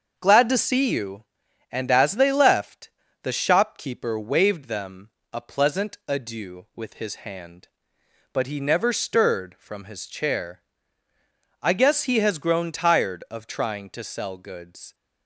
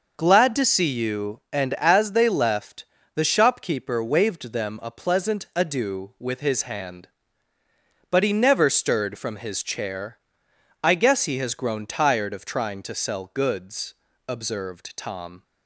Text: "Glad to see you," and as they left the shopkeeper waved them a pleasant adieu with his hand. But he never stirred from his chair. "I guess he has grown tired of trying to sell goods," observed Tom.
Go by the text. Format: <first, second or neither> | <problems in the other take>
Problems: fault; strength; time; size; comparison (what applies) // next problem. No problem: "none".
second | starts louder than the rest; until 1.1 s; 6.5 dB // pauses between "left" and "the"; slight; at 2.8 s; 0.32 s long; slight in the second // pauses between "them" and "a"; slight; at 5.1 s; 0.20 s long // stops before "observed Tom"; at 14.9 s